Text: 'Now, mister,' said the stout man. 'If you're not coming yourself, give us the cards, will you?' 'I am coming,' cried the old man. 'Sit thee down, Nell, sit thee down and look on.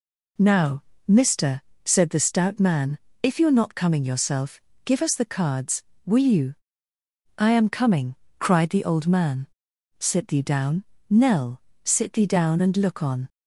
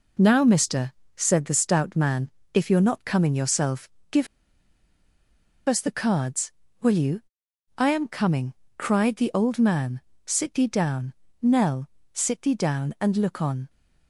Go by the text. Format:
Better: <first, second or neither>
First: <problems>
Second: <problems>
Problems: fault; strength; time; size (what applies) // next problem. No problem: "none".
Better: first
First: none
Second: pauses between "give" and "us"; strong; at 4.2 s; 1.4 s long